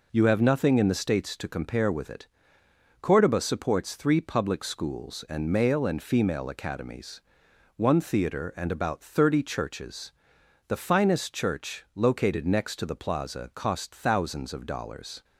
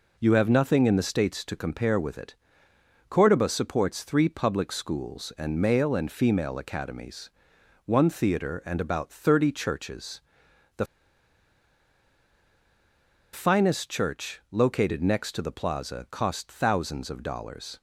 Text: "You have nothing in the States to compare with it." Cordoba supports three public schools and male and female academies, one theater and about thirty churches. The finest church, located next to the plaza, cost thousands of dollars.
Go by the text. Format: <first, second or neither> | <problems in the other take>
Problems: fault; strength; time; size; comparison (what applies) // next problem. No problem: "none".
first | pauses between "The" and "finest"; strong; at 10.8 s; 2.4 s long